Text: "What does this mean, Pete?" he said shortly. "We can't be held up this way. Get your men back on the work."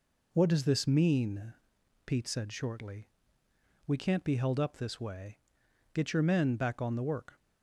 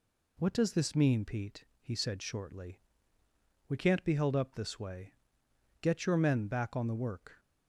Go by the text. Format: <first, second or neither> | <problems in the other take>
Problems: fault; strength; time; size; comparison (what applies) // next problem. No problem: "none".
second | skips "he"; at 2.2 s